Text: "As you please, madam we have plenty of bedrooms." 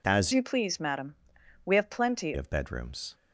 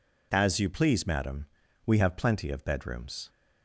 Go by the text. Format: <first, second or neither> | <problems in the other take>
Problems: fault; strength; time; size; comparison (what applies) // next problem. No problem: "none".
second | changes voice from "you" to "plenty"; from 0.3 to 2.3 s; 2.0 s long // pauses between "madam" and "we"; noticeable; at 1.1 s; 0.50 s long; also in the second